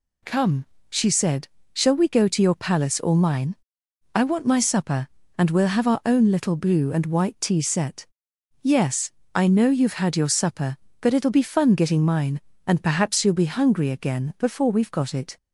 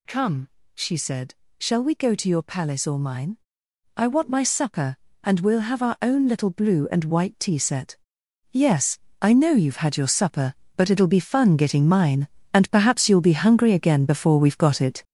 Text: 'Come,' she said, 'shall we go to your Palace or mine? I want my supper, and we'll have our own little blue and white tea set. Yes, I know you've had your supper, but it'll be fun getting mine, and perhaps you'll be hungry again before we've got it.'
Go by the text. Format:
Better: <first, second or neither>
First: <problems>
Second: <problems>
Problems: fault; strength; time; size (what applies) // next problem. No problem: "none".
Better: first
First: none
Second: gets louder; throughout; 7 dB